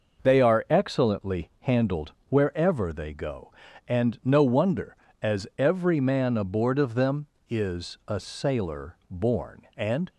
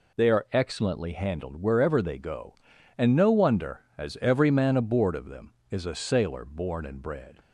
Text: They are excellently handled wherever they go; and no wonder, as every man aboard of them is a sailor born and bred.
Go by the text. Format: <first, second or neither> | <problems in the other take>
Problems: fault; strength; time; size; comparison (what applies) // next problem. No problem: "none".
second | pauses between "handled" and "wherever"; slight; at 2.1 s; 0.16 s long // stops before "bred"; at 10.0 s